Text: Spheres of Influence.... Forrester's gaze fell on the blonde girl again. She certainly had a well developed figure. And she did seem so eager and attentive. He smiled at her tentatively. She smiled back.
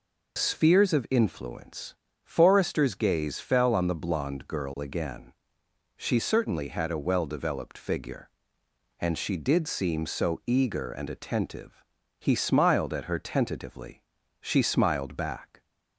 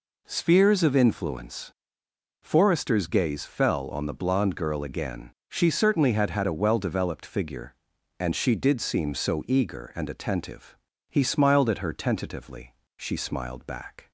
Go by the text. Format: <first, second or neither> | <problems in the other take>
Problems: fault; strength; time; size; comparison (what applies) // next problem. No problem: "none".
first | says "had" twice; at 6.3 s